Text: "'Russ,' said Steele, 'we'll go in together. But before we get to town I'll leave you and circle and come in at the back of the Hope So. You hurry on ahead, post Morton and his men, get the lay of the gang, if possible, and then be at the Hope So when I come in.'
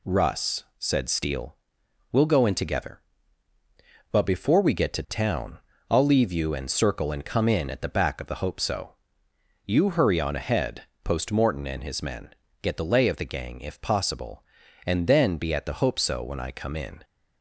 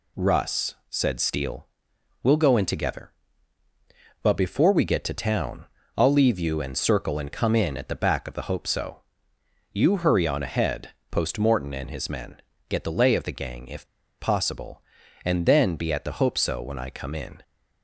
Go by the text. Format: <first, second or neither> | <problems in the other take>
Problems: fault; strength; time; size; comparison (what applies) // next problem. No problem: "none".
first | pauses between "town" and "I'll"; slight; at 5.6 s; 0.30 s long; slight in the first // pauses between "if" and "possible"; slight; at 13.8 s; 0.33 s long